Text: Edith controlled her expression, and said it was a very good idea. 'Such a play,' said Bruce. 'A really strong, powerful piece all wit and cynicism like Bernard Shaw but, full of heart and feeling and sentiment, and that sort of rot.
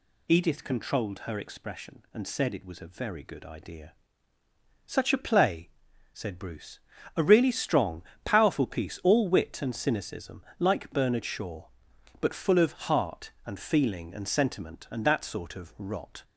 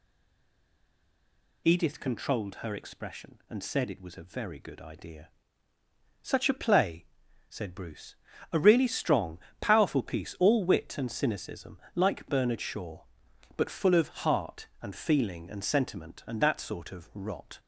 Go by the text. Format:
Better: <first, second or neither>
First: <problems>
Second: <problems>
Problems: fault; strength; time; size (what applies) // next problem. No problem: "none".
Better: first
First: pauses between "cynicism" and "like"; slight; at 10.4 s; 0.18 s long // pauses between "of" and "heart"; slight; at 12.7 s; 0.16 s long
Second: stays silent before the first word; noticeable; until 1.6 s; 1.6 s long // pauses between "cynicism" and "like"; slight; at 11.7 s; 0.18 s long // pauses between "of" and "heart"; slight; at 14.0 s; 0.16 s long